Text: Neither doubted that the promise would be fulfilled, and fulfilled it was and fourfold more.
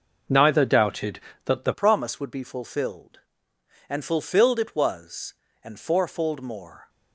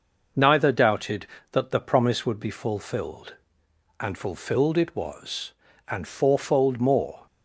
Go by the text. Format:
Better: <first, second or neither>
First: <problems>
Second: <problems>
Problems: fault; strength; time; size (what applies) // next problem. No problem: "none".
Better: second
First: changes voice at "promise"; from 1.7 s on; 5.1 s long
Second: none